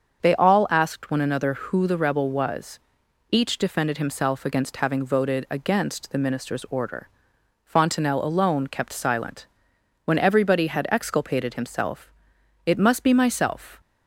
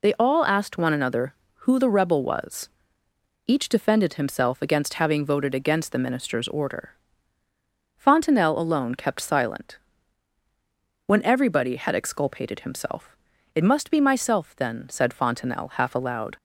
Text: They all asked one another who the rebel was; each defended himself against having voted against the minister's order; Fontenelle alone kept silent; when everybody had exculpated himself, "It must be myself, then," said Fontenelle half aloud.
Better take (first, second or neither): second